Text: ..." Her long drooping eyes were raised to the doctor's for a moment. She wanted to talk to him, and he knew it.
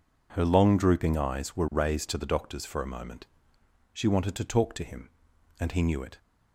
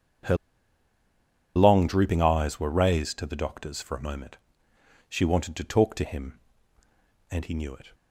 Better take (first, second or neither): first